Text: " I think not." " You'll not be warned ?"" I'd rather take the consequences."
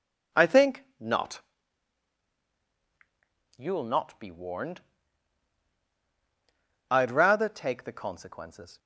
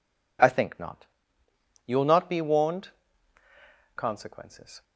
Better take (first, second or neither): first